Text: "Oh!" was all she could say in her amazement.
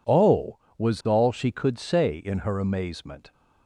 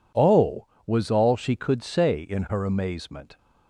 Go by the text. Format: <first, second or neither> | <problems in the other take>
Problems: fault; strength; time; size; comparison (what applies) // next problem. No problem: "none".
neither | none